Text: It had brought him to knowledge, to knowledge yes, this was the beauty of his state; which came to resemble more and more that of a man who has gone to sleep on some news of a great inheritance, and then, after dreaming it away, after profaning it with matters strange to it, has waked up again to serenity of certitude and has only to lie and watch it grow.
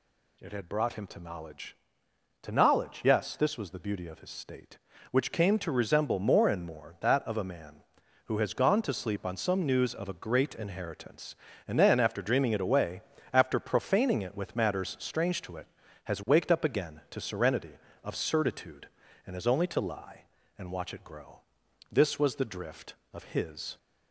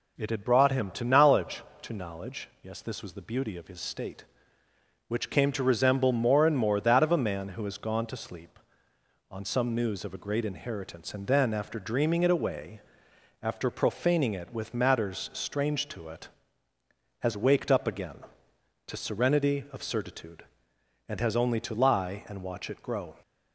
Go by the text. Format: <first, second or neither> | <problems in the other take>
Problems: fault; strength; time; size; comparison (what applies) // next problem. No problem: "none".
second | goes on to say "This was the drift of his"; strong; from 21.9 s on; 1.8 s long